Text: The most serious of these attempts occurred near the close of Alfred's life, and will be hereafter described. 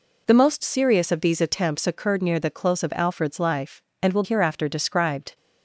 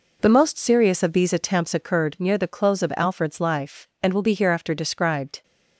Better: second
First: skips "be"; at 4.2 s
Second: none

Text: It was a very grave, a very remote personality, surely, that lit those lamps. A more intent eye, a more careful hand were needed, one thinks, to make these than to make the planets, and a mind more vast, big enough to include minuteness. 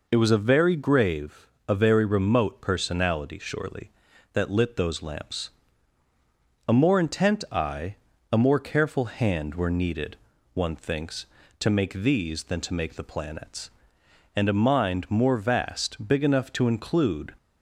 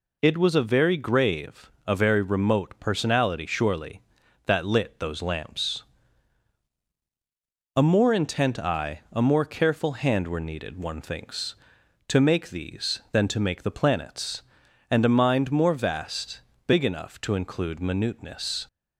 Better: second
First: stops before "minuteness"; at 17.3 s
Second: none

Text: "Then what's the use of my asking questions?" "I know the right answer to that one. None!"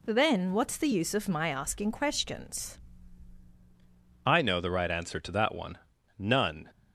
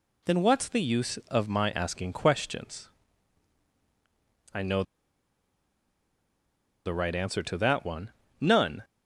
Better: first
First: none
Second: pauses between "know" and "the"; strong; at 4.8 s; 2.0 s long

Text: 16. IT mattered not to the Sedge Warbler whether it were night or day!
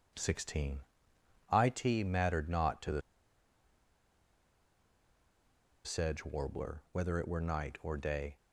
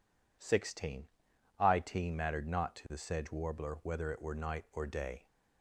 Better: second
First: pauses between "the" and "Sedge"; strong; at 3.0 s; 2.8 s long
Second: none

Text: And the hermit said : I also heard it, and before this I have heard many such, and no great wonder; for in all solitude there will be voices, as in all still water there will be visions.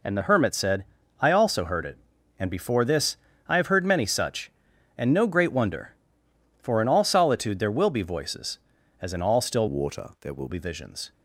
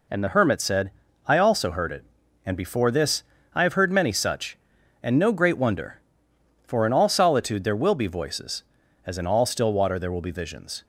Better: second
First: pauses between "this" and "I"; slight; at 3.1 s; 0.30 s long // changes voice from "water" to "will"; from 9.6 to 10.4 s; 0.8 s long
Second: pauses between "this" and "I"; slight; at 3.2 s; 0.30 s long

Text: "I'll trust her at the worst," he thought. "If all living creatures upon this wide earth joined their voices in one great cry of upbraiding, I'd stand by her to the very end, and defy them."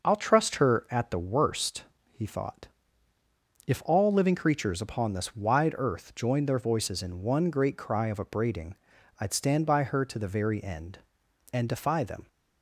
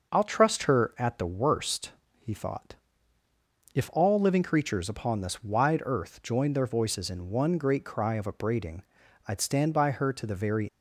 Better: first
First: none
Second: stops before "end and defy them"; at 10.6 s

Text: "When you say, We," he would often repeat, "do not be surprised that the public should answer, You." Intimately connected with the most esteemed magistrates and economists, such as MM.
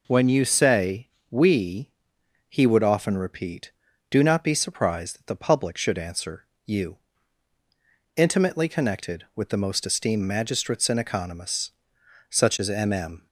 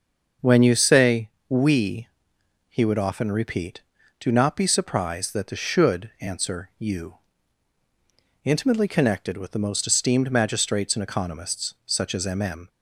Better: first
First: none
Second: starts louder than the rest; until 1.6 s; 6 dB // skips "public"; at 5.5 s

